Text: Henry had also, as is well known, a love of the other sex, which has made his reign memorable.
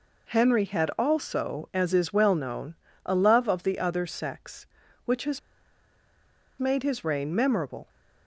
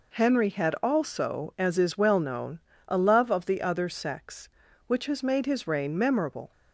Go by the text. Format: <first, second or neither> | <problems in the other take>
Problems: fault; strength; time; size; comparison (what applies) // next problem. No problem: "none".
second | pauses between "has" and "made"; at 5.3 s; 1.1 s long